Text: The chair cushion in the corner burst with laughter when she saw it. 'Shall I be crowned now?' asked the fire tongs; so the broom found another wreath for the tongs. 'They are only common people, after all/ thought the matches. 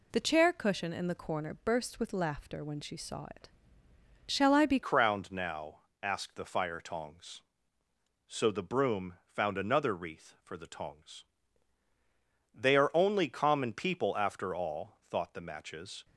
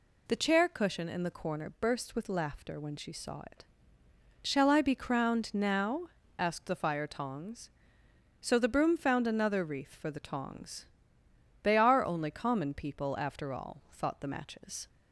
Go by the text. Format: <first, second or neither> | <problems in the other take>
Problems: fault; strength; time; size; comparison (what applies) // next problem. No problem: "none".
second | changes voice at "crowned"; from 4.8 s on; 11.2 s long